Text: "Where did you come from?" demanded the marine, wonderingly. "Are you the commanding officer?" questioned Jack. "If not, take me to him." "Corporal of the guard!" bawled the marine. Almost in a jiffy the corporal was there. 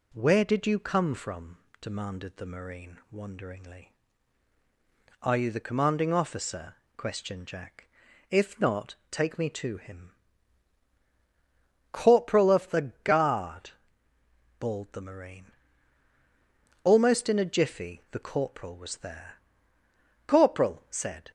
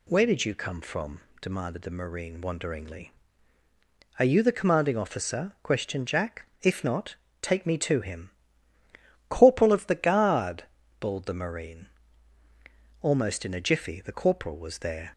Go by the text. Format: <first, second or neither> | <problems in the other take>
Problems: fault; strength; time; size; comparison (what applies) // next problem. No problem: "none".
second | goes on to say "Corporal said"; noticeable; from 20.2 s on; 1.0 s long